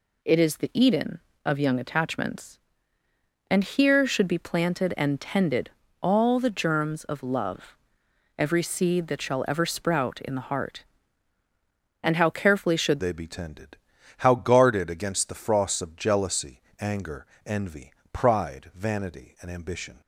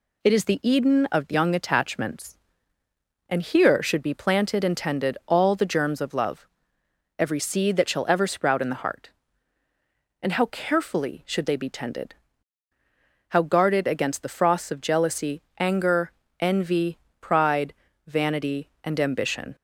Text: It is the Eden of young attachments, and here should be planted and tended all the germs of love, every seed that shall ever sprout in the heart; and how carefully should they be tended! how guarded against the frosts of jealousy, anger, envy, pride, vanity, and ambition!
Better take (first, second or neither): second